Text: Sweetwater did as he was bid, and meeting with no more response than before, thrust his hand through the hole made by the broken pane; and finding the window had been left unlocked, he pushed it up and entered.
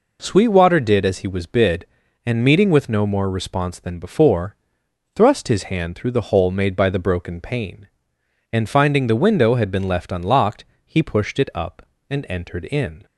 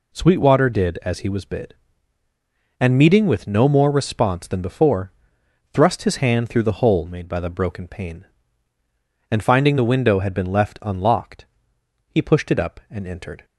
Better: second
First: goes on to say "In"; slight; from 12.6 s on; 0.40 s long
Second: none

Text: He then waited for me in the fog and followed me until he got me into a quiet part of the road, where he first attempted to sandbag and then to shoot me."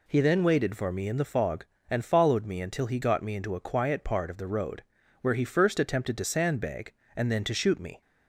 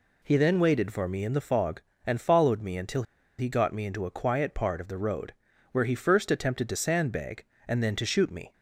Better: first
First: none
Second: pauses between "until" and "he"; slight; at 3.0 s; 0.35 s long

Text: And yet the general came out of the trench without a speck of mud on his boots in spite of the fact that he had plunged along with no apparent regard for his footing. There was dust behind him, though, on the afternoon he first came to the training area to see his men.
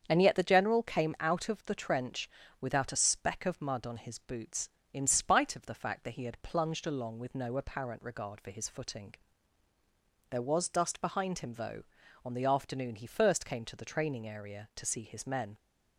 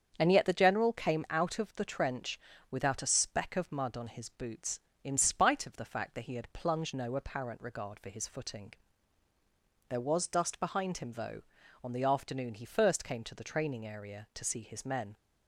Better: first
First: starts louder than the rest; strong; until 1.0 s; 7.5 dB // pauses between "trench" and "without"; slight; at 2.2 s; 0.32 s long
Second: starts louder than the rest; strong; until 1.1 s; 7.5 dB // pauses between "trench" and "without"; slight; at 2.3 s; 0.32 s long // skips "along with"; at 6.9 s

